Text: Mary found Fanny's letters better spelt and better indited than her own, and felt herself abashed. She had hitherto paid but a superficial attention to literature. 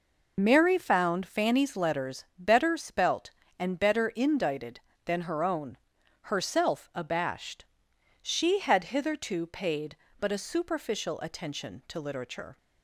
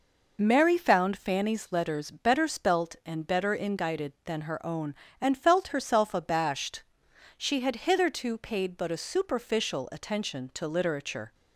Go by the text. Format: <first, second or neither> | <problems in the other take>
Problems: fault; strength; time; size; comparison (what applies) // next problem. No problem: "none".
second | skips "and felt"; at 5.9 s